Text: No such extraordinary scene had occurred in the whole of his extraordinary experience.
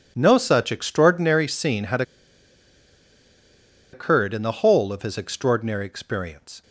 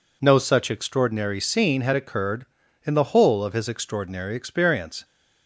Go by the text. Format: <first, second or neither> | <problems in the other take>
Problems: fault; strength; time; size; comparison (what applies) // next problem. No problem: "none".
second | pauses between "had" and "occurred"; strong; at 2.0 s; 1.9 s long